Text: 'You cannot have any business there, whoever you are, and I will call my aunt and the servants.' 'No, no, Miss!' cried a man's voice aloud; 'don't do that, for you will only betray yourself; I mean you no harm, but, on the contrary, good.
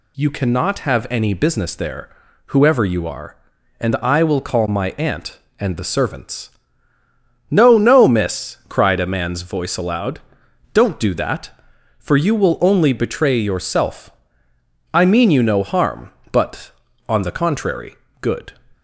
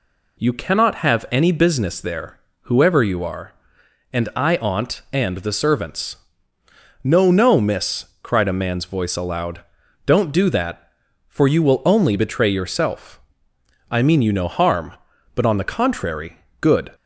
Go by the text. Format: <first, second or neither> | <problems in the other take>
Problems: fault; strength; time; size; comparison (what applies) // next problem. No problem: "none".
first | skips "will call my"; at 4.5 s